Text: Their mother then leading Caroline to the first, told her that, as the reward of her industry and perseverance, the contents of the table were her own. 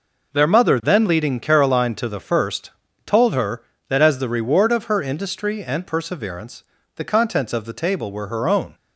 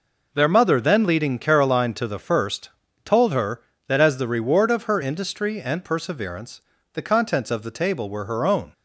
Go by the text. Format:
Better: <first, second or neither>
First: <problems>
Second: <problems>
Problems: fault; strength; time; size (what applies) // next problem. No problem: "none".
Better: neither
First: none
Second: none